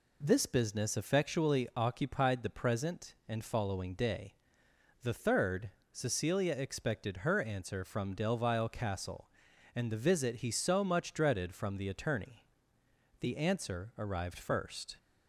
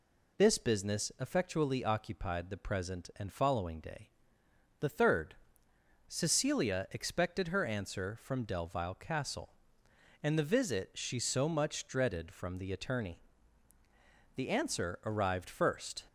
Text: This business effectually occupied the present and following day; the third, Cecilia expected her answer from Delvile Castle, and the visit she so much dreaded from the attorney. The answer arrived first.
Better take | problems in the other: second | says "he" for "she"; at 10.4 s

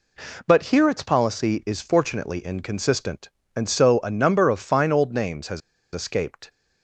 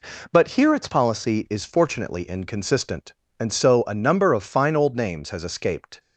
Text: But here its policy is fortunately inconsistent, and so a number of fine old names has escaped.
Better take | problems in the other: second | pauses between "has" and "escaped"; slight; at 5.6 s; 0.32 s long

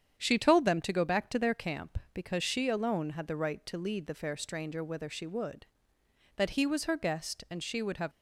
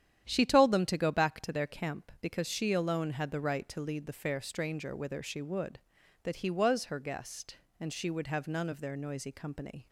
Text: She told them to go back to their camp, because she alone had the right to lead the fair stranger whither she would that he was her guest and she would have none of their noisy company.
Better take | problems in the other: second | starts louder than the rest; strong; until 1.1 s; 8.5 dB; strong in the second // stops before "none of their noisy company"; at 8.1 s

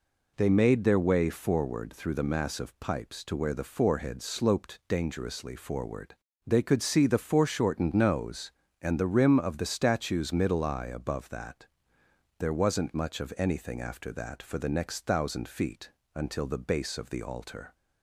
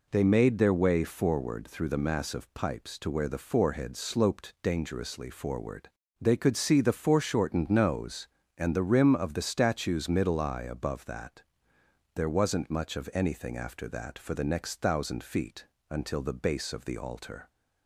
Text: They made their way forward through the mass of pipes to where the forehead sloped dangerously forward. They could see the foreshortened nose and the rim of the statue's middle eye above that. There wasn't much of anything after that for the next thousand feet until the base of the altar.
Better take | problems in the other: neither | pauses between "feet" and "until"; slight; the same in both

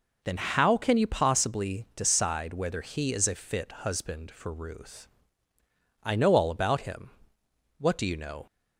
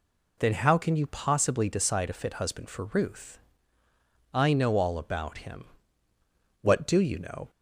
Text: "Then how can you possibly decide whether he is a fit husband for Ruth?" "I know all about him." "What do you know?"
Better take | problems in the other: first | skips "whether he is"; at 2.0 s

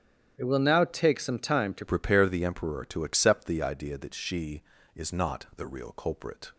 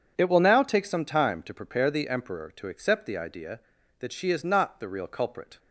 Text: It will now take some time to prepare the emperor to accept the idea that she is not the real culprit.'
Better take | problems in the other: second | starts louder than the rest; strong; until 1.3 s; 9.5 dB // changes voice at "prepare"; from 1.8 s on; 4.7 s long

